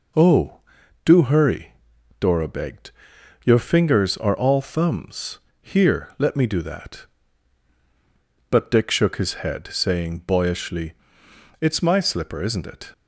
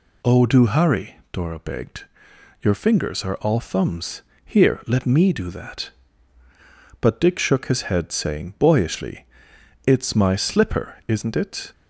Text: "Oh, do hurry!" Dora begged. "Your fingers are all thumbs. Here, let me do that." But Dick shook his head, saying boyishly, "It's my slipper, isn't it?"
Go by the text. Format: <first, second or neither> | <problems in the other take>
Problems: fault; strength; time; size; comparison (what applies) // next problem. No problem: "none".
neither | none